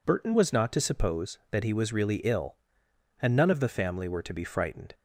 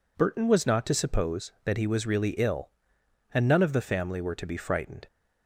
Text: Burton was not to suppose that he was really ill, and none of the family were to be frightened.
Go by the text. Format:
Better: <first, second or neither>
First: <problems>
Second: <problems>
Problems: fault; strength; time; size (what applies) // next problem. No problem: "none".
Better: neither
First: none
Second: none